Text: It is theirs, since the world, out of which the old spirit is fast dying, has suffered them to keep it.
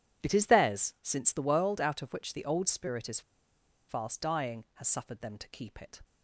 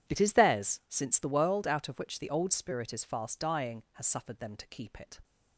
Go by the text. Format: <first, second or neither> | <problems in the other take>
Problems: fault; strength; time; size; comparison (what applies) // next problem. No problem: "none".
second | pauses between "is" and "fast"; noticeable; at 3.2 s; 0.68 s long